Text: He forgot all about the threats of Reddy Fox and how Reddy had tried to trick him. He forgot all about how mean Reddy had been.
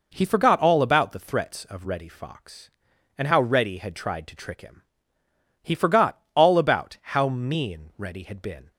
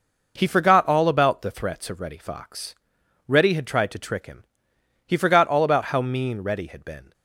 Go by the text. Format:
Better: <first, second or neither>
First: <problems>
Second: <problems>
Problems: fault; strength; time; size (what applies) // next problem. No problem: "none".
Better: first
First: none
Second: skips "and how"; at 3.0 s